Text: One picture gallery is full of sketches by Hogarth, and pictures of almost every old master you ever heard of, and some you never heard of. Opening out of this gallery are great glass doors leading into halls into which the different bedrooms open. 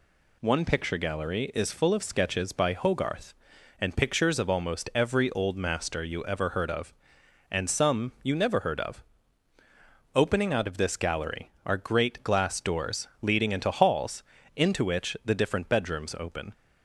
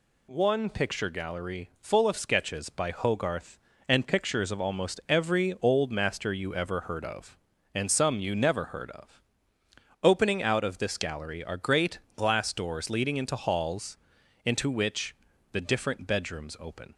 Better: first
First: pauses between "halls" and "into"; slight; at 14.2 s; 0.32 s long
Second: skips "is"; at 1.7 s // pauses between "great" and "glass"; slight; at 11.9 s; 0.18 s long // pauses between "halls" and "into"; noticeable; at 13.9 s; 0.48 s long // pauses between "which" and "the"; slight; at 15.1 s; 0.36 s long

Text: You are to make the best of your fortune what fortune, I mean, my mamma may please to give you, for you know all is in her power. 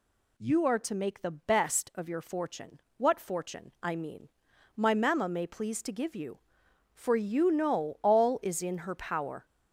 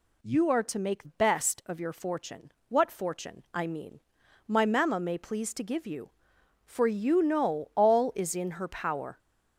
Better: first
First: pauses between "fortune" and "what"; slight; at 2.8 s; 0.16 s long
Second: skips "the"; at 1.0 s // pauses between "fortune" and "what"; slight; at 2.5 s; 0.16 s long

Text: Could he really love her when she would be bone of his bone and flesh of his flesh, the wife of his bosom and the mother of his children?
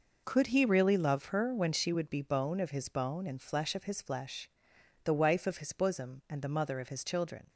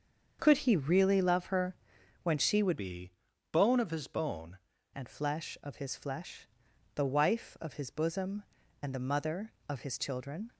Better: first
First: none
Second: starts louder than the rest; until 1.4 s; 7 dB // pauses between "her" and "when"; noticeable; at 1.7 s; 0.46 s long // changes voice from "be" to "bone"; from 2.7 to 4.5 s; 1.8 s long // pauses between "be" and "bone"; at 3.1 s; 0.40 s long

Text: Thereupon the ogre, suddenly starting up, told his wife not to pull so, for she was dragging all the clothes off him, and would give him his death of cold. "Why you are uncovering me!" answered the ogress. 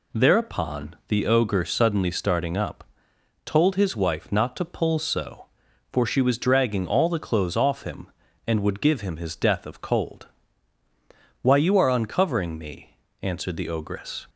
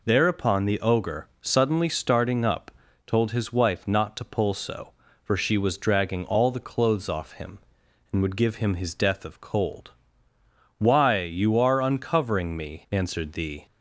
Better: first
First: none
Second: stops before "ogress"; at 13.6 s

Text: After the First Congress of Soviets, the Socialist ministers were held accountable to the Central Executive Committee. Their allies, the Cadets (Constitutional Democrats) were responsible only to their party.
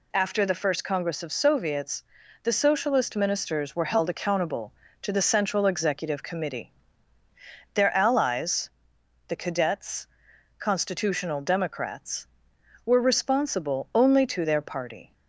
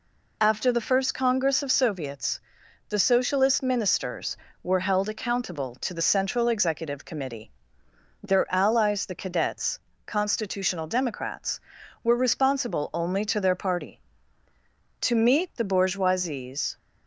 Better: first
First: none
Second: goes on to say "To meet the bourgeoisie's"; strong; from 15.0 s on; 1.7 s long

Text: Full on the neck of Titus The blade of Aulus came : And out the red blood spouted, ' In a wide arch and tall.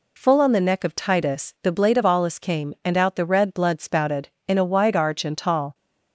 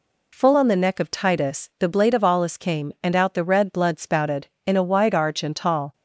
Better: neither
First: none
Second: none

